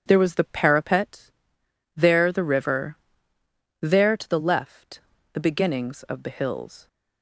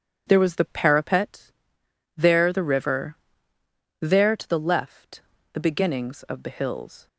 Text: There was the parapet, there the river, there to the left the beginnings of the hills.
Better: neither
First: pauses between "left" and "the"; slight; at 4.9 s; 0.34 s long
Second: pauses between "left" and "the"; slight; at 5.2 s; 0.32 s long

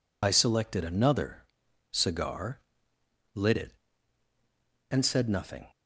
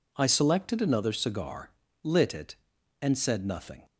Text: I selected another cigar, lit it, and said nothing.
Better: second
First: loses the start of "I"; at 0.2 s; 55 ms // pauses between "another" and "cigar"; noticeable; at 1.4 s; 0.48 s long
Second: none

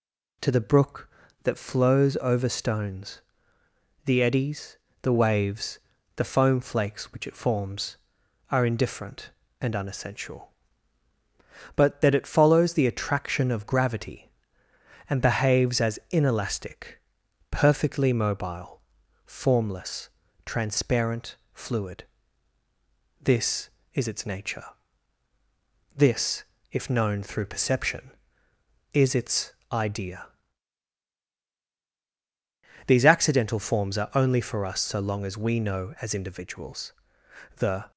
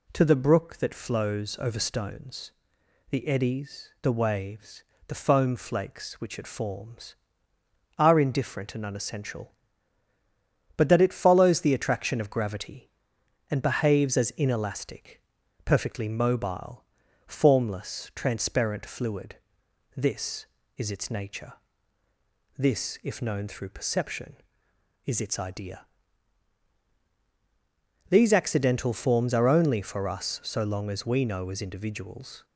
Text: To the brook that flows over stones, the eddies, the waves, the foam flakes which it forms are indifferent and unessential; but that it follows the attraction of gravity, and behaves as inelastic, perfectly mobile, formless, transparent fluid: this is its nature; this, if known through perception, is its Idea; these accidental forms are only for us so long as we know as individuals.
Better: second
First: pauses between "transparent" and "fluid"; slight; at 21.3 s; 0.18 s long // pauses between "its" and "Idea"; slight; at 29.5 s; 0.20 s long // goes on to say "The"; slight; from 37.5 s on; 0.34 s long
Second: none

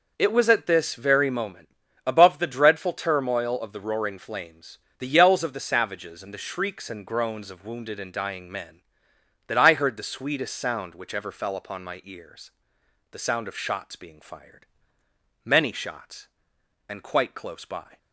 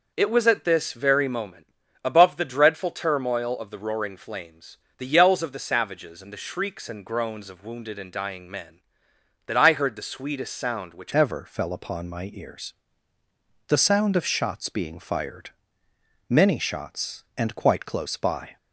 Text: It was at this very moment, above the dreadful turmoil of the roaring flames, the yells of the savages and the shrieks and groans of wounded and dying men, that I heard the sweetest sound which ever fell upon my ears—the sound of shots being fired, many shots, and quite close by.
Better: first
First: none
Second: changes voice at "ever"; from 11.1 s on; 7.4 s long

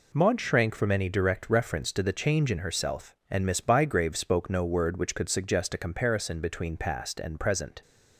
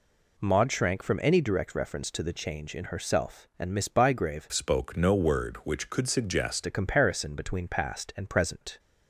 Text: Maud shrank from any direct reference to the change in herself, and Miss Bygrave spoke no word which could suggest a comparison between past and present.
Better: first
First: none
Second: changes voice from "spoke" to "suggest"; from 4.5 to 6.6 s; 2.1 s long

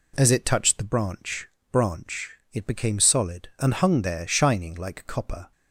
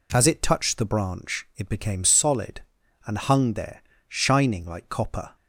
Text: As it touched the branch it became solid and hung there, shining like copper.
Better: second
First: says "branch" twice; at 1.7 s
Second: none

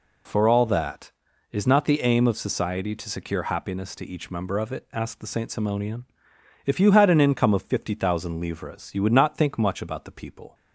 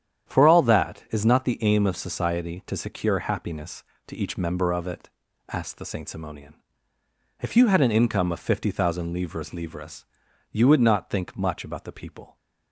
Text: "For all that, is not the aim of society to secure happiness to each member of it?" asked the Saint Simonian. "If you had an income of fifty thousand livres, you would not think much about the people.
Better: first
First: none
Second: starts louder than the rest; strong; until 1.3 s; 9.5 dB // says "livres" twice; at 9.5 s

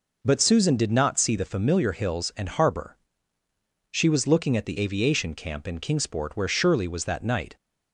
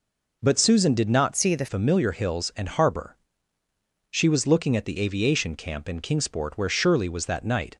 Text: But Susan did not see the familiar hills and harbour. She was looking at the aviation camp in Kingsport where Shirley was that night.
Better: first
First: none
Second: changes voice from "see" to "the"; from 1.3 to 1.6 s; 0.3 s long

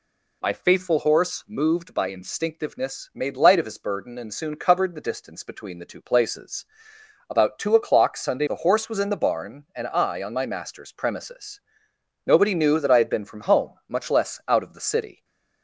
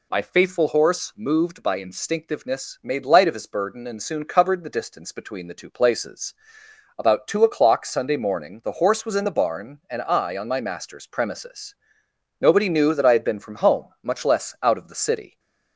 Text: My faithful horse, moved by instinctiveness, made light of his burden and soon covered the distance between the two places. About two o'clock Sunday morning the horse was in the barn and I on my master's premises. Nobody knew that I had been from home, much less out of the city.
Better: second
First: skips "morning"; at 8.4 s // stays silent after the last word; slight; from 15.1 s on; 0.5 s long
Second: none

